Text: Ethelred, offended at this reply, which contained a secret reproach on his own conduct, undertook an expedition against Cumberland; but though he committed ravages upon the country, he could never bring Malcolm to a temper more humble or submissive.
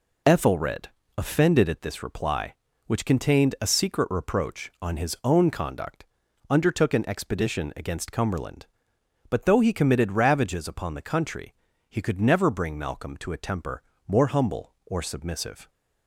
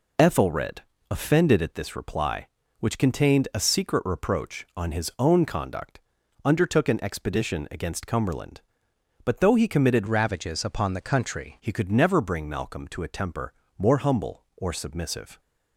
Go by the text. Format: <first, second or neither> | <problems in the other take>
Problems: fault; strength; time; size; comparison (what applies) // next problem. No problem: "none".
first | changes voice from "ravages" to "country"; from 10.0 to 11.5 s; 1.5 s long // pauses between "temper" and "more"; slight; at 13.5 s; 0.24 s long; slight in the first